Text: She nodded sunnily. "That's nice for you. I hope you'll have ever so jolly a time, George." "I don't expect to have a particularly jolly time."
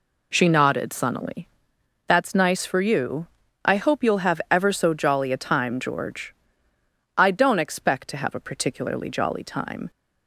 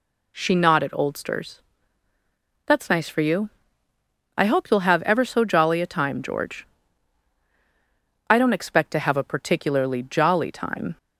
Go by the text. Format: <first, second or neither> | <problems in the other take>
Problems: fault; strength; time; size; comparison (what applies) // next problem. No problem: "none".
first | says "oldsters" for "sunnily"; at 0.9 s